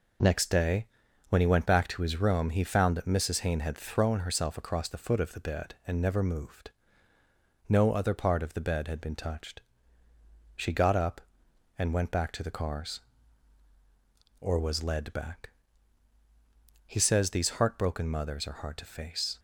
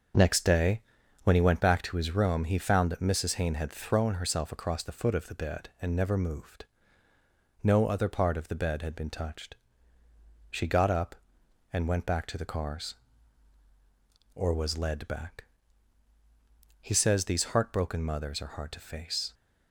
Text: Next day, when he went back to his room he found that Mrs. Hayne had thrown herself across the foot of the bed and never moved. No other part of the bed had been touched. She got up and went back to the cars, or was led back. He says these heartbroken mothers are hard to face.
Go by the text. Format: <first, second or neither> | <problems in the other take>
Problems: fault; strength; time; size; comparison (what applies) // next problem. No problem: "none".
first | starts louder than the rest; until 1.6 s; 6.5 dB